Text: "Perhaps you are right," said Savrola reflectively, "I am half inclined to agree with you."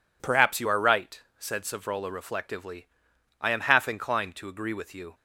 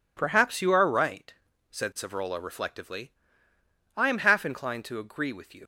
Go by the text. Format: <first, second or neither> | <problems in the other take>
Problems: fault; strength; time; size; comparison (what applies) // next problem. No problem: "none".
first | leaves "you" unfinished; at 5.6 s; 70 ms